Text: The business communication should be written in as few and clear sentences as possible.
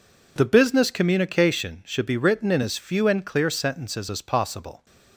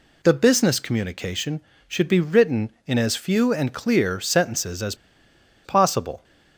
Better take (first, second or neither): first